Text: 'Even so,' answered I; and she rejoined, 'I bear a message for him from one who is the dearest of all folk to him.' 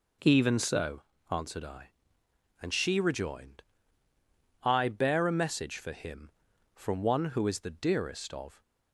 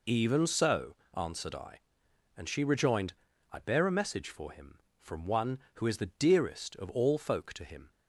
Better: second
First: stops before "all folk to him"; at 8.6 s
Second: none

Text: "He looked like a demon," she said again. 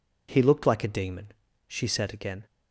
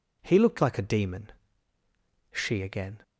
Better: first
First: none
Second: skips "said"; at 2.6 s

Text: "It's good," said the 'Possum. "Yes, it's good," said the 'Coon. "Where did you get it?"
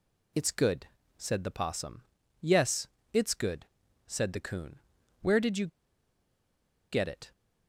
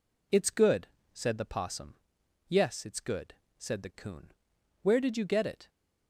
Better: second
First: pauses between "you" and "get"; strong; at 5.6 s; 1.2 s long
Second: none

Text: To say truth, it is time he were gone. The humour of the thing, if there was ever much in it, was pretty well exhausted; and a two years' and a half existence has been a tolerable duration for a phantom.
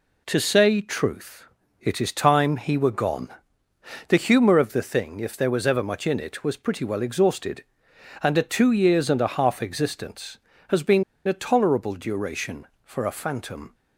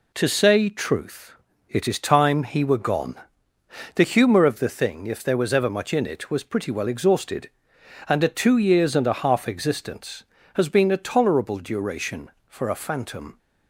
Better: second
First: pauses between "been" and "a"; slight; at 11.0 s; 0.22 s long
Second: none

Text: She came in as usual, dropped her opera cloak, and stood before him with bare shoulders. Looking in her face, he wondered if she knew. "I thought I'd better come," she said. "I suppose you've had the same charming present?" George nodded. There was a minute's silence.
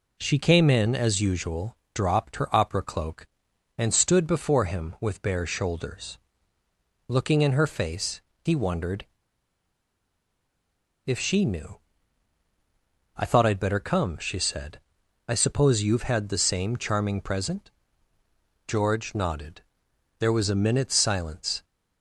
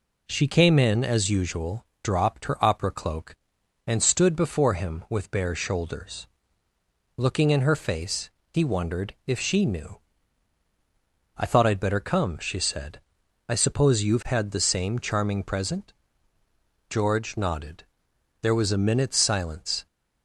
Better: second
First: pauses between "wondered" and "if"; strong; at 9.0 s; 1.9 s long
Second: none

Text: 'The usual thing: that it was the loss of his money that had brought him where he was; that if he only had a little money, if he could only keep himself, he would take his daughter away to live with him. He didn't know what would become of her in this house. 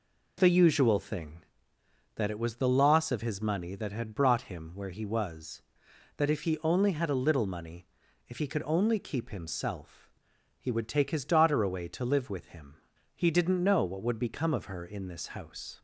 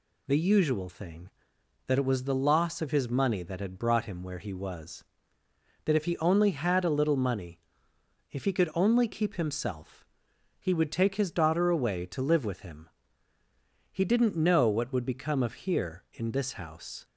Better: first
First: none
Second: says "here" for "her"; at 15.5 s

